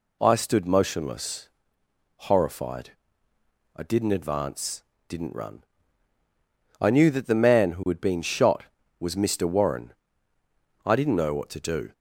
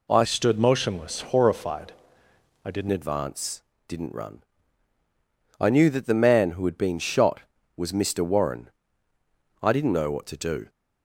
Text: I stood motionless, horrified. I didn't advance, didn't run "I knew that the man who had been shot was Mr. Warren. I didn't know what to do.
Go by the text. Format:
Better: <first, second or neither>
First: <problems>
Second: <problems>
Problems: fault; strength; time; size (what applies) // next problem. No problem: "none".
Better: first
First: pauses between "run" and "I"; at 5.6 s; 1.1 s long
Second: changes voice from "stood" to "didn't"; from 0.2 to 2.8 s; 2.6 s long // pauses between "run" and "I"; at 4.4 s; 1.1 s long